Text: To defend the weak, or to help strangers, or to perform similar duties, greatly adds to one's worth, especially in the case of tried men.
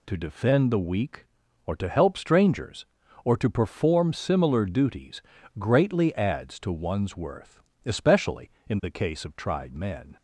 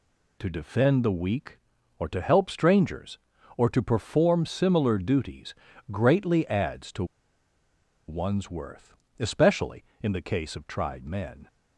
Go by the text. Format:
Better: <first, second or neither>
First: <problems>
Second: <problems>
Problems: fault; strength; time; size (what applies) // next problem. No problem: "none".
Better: first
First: none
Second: pauses between "to" and "one's"; at 7.0 s; 1.0 s long